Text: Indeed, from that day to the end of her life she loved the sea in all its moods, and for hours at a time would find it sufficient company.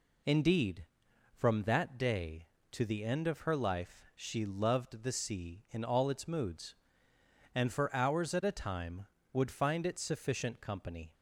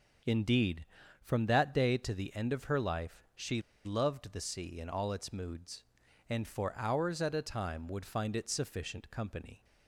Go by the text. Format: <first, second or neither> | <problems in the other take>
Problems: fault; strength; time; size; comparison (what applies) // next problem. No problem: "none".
first | starts louder than the rest; noticeable; until 1.6 s; 6 dB // pauses between "she" and "loved"; slight; at 3.6 s; 0.23 s long